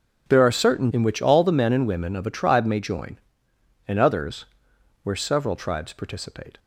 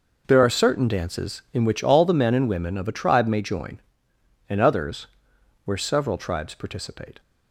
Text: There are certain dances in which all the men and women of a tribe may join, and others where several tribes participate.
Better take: second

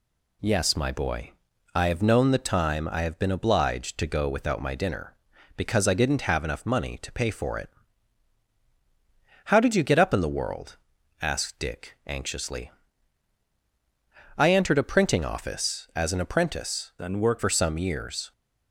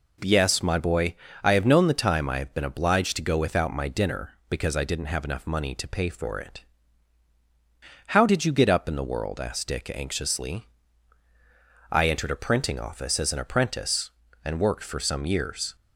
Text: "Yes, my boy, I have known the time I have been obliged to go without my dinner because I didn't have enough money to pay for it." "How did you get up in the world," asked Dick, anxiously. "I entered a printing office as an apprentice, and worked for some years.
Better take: second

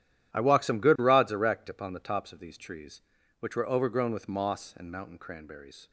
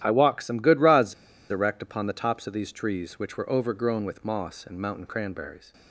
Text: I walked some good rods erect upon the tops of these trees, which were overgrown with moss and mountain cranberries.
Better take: first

